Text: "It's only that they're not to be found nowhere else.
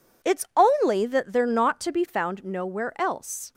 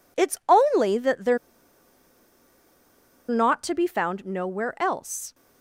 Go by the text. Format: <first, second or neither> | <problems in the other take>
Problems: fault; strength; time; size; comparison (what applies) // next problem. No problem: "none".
first | pauses between "they're" and "not"; strong; at 1.3 s; 1.9 s long